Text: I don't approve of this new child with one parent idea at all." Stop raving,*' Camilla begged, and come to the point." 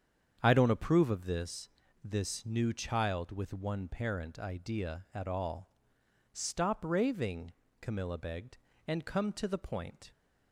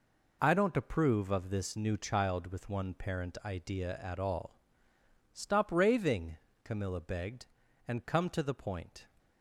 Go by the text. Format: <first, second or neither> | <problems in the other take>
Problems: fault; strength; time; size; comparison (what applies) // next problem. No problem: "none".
second | starts louder than the rest; strong; until 1.4 s; 8 dB // says "this" twice; at 2.0 s